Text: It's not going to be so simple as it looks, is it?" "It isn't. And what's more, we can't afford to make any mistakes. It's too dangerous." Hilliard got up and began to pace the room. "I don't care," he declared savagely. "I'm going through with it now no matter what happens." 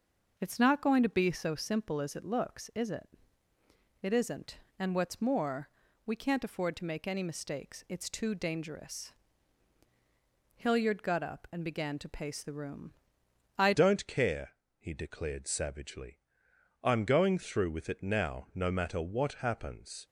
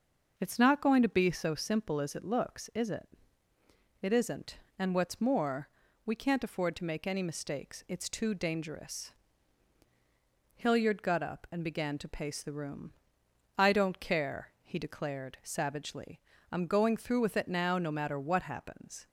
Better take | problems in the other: second | starts louder than the rest; noticeable; until 1.3 s; 6 dB; noticeable in the second // changes voice at "don't"; from 13.7 s on; 6.3 s long

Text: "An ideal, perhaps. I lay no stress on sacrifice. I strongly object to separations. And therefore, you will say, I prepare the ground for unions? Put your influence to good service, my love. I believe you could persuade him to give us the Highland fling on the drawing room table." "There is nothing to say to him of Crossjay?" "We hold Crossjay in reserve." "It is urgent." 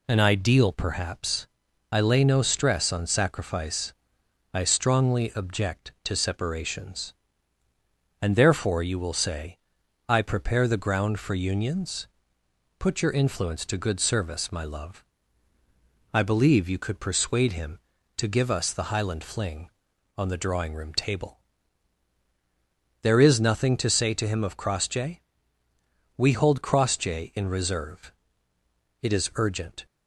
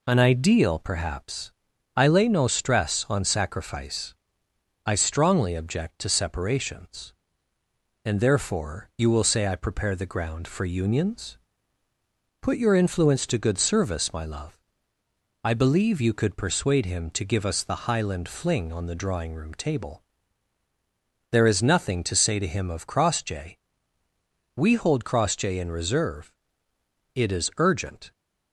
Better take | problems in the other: neither | none

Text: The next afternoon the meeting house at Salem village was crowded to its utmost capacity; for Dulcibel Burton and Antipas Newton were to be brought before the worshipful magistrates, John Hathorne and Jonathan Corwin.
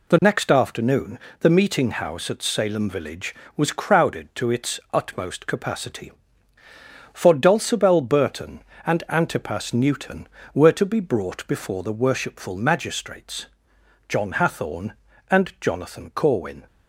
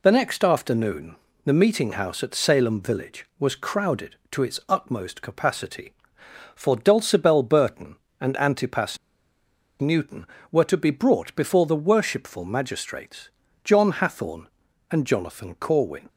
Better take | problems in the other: first | pauses between "afternoon" and "the"; slight; at 1.1 s; 0.28 s long; slight in the first // pauses between "Antipas" and "Newton"; noticeable; at 8.9 s; 0.84 s long

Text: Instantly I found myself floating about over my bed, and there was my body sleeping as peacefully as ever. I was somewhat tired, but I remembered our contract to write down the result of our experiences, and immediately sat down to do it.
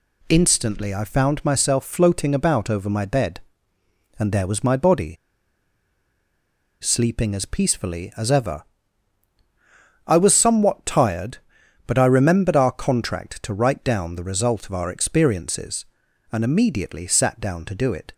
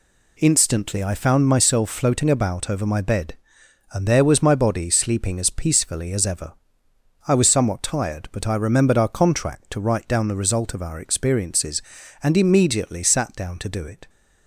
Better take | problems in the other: second | pauses between "body" and "sleeping"; strong; at 5.1 s; 1.6 s long

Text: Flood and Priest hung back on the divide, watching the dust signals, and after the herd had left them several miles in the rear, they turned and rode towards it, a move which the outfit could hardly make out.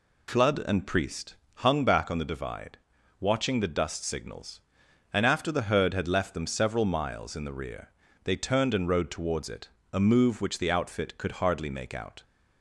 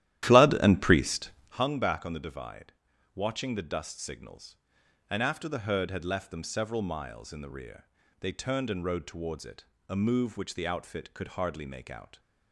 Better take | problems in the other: first | starts louder than the rest; strong; until 1.6 s; 13 dB // pauses between "Priest" and "hung"; slight; at 1.2 s; 0.32 s long; slight in the first

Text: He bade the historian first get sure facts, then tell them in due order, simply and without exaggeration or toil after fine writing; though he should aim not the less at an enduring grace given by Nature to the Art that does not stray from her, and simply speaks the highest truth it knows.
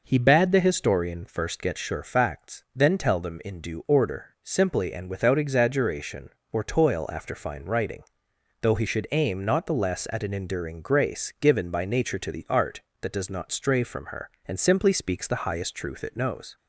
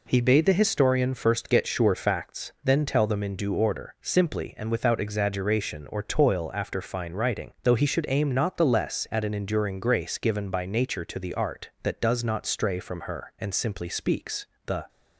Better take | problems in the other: first | pauses between "speaks" and "the"; slight; at 14.4 s; 0.22 s long // stops before "highest truth it knows"; at 14.8 s

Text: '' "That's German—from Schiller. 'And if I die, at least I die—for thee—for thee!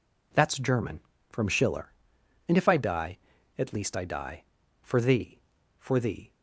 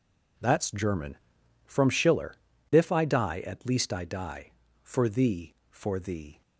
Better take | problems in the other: first | skips "And"; at 2.5 s

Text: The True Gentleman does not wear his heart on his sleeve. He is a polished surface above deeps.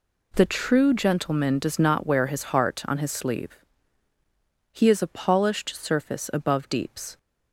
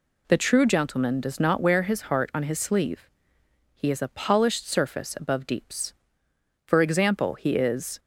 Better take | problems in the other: first | goes on to say "For example he is"; from 6.6 s on; 1.3 s long

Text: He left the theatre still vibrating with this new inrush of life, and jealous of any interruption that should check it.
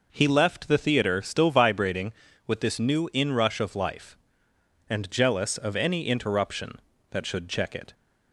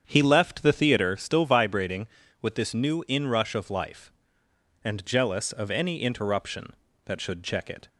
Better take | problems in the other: first | starts louder than the rest; strong; until 1.1 s; 8 dB

